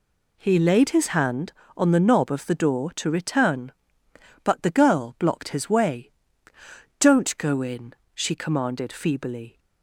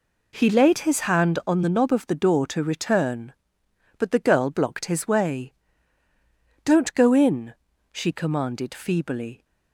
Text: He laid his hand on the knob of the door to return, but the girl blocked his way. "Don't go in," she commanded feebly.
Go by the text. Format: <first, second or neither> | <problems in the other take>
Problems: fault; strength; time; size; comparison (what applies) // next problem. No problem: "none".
neither | none